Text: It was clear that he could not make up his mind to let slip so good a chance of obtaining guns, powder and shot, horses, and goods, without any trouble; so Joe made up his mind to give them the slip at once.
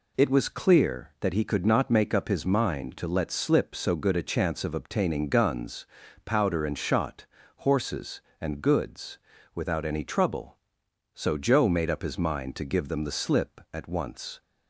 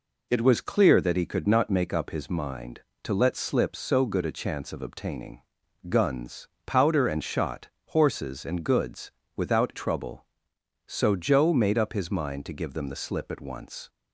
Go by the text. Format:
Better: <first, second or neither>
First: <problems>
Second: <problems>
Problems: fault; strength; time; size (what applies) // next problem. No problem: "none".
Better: first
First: none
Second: pauses between "obtaining" and "guns"; noticeable; at 5.4 s; 0.48 s long // skips "any"; at 9.7 s